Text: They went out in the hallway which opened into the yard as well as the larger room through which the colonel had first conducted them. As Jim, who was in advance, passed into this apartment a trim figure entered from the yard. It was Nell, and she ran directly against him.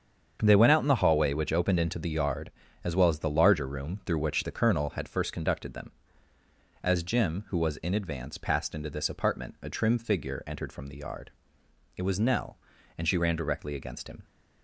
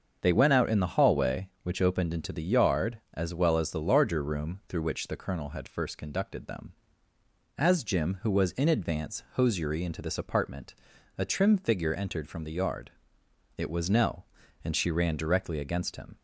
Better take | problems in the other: first | starts louder than the rest; until 1.2 s; 7 dB; strong in the first // says "hosiery" for "passed"; at 9.3 s // pauses between "apartment" and "a"; at 10.7 s; 0.44 s long

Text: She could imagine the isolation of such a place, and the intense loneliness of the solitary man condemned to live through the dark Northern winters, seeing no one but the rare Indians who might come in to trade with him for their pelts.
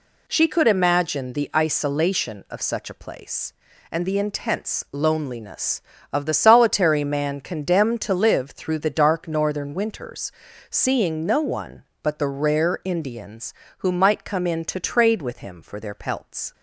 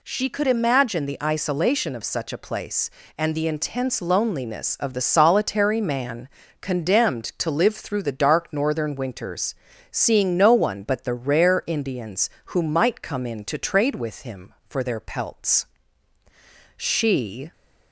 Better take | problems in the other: first | pauses between "man" and "condemned"; slight; at 6.2 s; 0.32 s long // goes on to say "She"; noticeable; from 16.7 s on; 0.76 s long

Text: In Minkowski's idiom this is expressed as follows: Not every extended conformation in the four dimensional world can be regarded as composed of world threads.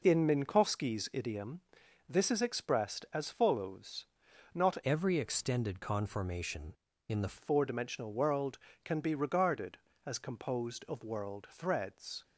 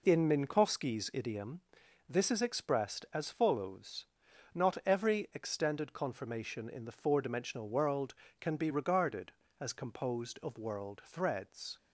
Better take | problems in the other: second | pauses between "idiom" and "this"; noticeable; at 1.6 s; 0.48 s long; noticeable in the second // changes voice from "every" to "the"; from 4.8 to 7.3 s; 2.5 s long

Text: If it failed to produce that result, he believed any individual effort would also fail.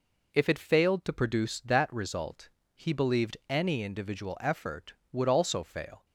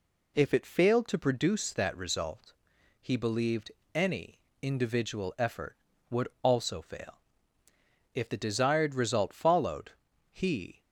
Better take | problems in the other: first | pauses between "believed" and "any"; slight; at 3.7 s; 0.24 s long // pauses between "any" and "individual"; slight; at 4.3 s; 0.24 s long // pauses between "would" and "also"; slight; at 6.2 s; 0.16 s long // goes on to say "If the desired result followed he"; strong; from 8.1 s on; 2.6 s long

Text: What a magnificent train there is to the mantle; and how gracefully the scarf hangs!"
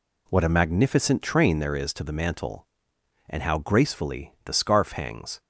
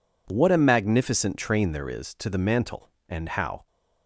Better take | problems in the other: first | stops before "gracefully the scarf hangs"; at 3.6 s

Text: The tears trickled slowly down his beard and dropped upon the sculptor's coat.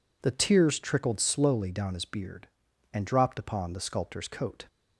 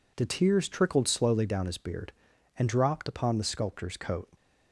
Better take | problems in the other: neither | none

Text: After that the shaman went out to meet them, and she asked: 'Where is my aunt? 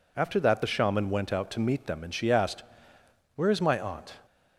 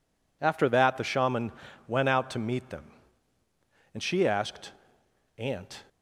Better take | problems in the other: first | pauses between "shaman" and "went"; slight; at 1.5 s; 0.36 s long // skips "Where is my"; at 5.0 s

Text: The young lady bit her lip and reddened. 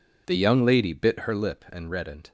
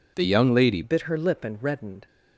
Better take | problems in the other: first | changes voice at "bit"; from 0.8 s on; 1.2 s long

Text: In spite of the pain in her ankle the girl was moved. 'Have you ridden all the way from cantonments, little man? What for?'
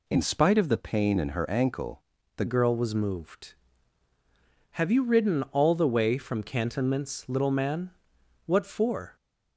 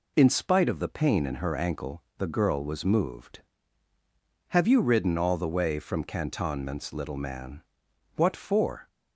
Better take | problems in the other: second | pauses between "ankle" and "the"; slight; at 2.0 s; 0.34 s long // changes voice at "girl"; from 2.4 s on; 6.7 s long

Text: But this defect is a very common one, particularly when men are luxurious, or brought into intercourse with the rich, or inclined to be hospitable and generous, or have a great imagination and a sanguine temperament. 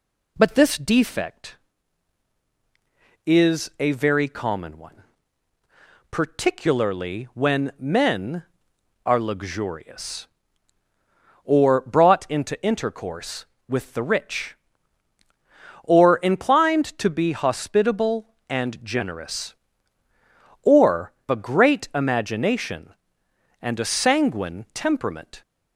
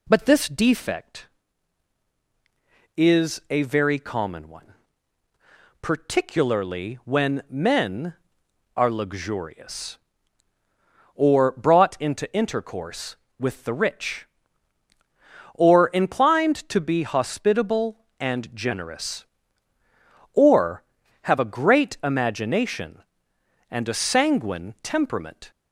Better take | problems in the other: second | skips "have"; at 21.2 s

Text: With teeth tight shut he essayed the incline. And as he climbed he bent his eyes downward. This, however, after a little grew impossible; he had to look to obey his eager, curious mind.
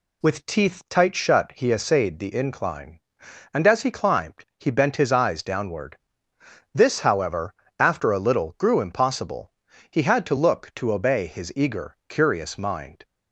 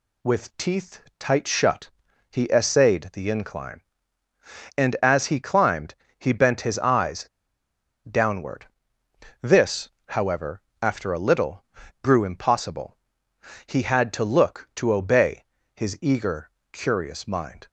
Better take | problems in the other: first | pauses between "teeth" and "tight"; slight; at 1.0 s; 0.18 s long // pauses between "shut" and "he"; at 1.8 s; 0.42 s long // pauses between "climbed" and "he"; slight; at 5.9 s; 0.24 s long // pauses between "eyes" and "downward"; noticeable; at 7.2 s; 0.83 s long // pauses between "little" and "grew"; slight; at 11.6 s; 0.36 s long // pauses between "obey" and "his"; slight; at 15.4 s; 0.32 s long

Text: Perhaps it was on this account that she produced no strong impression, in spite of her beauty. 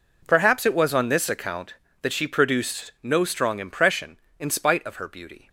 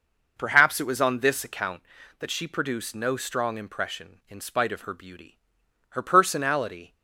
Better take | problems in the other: first | goes on to say "Her personality"; noticeable; from 5.8 s on; 1.0 s long

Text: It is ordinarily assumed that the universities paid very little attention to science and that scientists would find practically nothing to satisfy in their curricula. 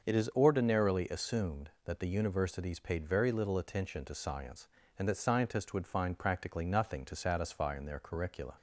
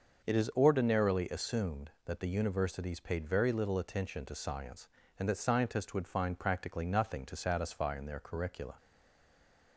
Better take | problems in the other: first | starts louder than the rest; until 1.3 s; 6.5 dB; also in the first // stays silent after the last word; from 8.7 s on; 1.0 s long

